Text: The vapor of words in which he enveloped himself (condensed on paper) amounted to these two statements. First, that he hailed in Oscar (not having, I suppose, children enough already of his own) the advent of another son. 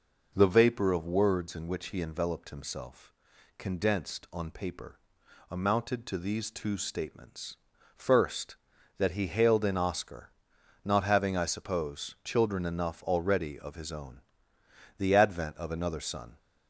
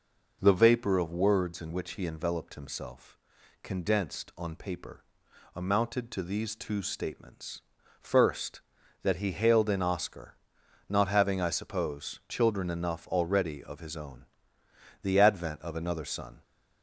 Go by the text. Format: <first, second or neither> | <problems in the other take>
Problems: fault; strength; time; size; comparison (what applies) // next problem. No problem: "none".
neither | none